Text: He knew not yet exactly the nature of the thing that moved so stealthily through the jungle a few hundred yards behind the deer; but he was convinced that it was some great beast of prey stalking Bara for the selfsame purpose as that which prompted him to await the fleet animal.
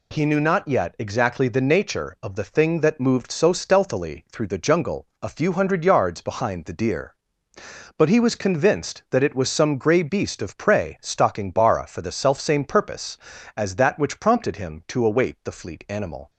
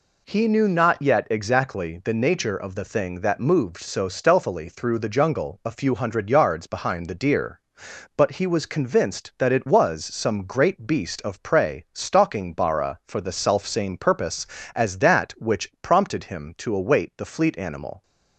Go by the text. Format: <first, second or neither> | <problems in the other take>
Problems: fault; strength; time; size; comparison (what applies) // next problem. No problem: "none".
second | pauses between "jungle" and "a"; slight; at 5.0 s; 0.16 s long // says "grey" for "great"; at 9.7 s